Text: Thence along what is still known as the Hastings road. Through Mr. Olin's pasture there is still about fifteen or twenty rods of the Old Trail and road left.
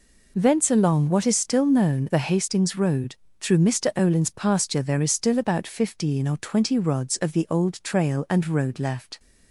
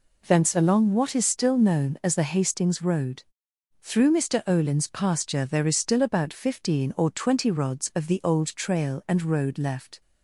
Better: second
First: skips "as"; at 2.0 s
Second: none

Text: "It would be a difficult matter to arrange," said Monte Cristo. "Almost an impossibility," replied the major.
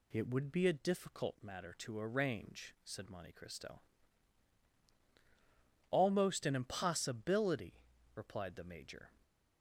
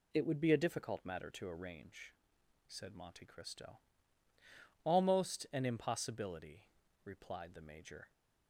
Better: neither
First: none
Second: none

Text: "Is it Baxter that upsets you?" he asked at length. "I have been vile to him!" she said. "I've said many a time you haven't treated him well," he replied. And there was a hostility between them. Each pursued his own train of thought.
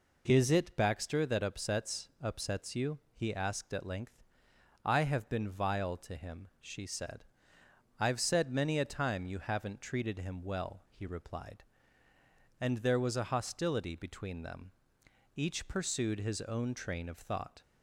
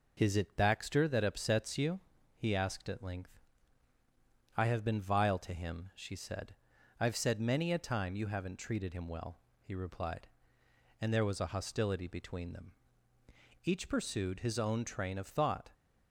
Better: second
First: says "upsets" twice; at 2.2 s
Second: none

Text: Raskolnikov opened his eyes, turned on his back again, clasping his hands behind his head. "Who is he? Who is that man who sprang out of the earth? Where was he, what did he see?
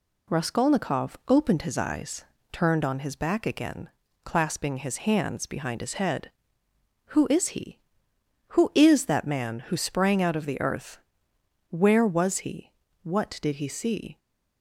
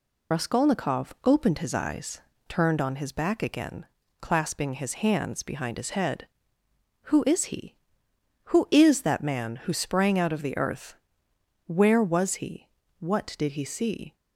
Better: first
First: none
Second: loses the start of "Raskolnikov"; at 0.3 s; 55 ms

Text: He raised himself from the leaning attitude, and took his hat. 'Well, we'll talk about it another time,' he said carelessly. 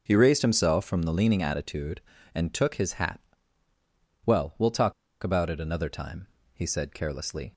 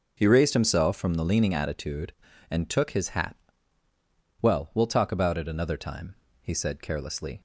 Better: second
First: pauses between "talk" and "about"; slight; at 4.9 s; 0.29 s long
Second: none

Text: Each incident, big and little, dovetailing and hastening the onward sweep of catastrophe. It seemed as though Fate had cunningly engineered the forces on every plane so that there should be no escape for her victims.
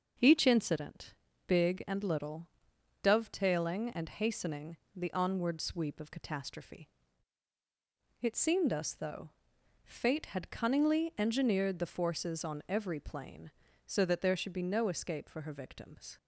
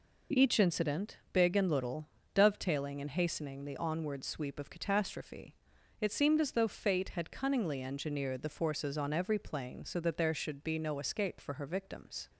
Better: second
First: starts louder than the rest; until 1.5 s; 6 dB // pauses between "hastening" and "the"; slight; at 4.7 s; 0.18 s long // says "us" for "as"; at 8.7 s // pauses between "though" and "Fate"; noticeable; at 9.2 s; 0.56 s long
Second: none

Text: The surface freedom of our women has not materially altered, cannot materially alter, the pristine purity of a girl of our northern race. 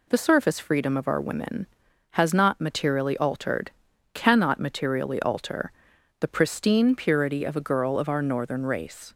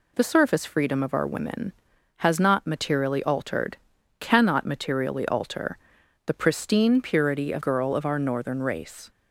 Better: first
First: none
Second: skips "a"; at 7.6 s

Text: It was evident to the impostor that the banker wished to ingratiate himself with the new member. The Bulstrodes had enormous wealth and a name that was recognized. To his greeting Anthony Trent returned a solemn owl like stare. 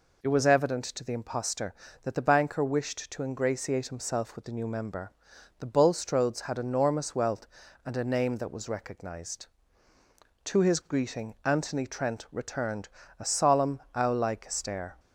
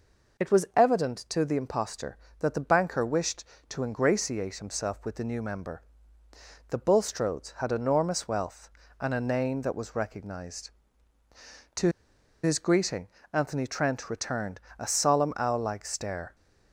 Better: first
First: pauses between "returned" and "a"; slight; at 12.8 s; 0.30 s long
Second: pauses between "To" and "his"; noticeable; at 11.8 s; 0.54 s long // pauses between "greeting" and "Anthony"; slight; at 13.0 s; 0.26 s long // pauses between "returned" and "a"; slight; at 14.5 s; 0.20 s long

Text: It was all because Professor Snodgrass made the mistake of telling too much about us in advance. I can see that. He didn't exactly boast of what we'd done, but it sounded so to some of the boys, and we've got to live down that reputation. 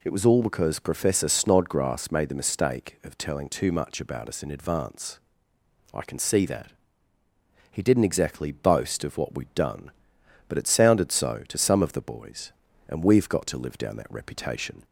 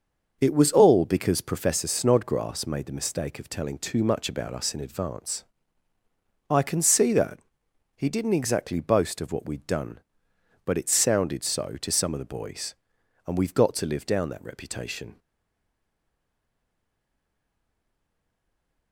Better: first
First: none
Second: starts louder than the rest; noticeable; until 1.4 s; 6 dB // stays silent after the last word; strong; from 15.1 s on; 3.8 s long

